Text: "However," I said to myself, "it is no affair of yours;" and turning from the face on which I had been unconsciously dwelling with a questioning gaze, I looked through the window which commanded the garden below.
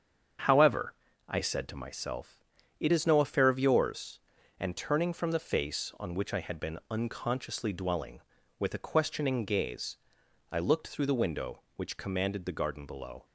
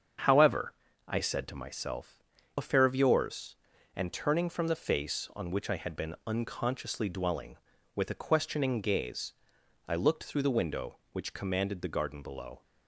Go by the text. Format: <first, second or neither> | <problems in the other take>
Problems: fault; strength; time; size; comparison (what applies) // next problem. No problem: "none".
first | starts louder than the rest; strong; until 1.5 s; 7 dB; strong in the first // skips "it is no"; at 2.3 s